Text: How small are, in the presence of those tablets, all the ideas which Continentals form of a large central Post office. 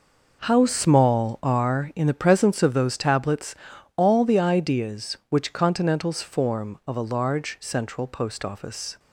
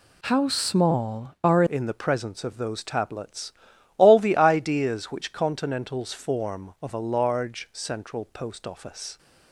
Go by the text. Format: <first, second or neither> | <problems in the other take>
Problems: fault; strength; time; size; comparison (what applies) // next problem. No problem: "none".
first | changes voice at "in"; from 1.6 s on; 7.5 s long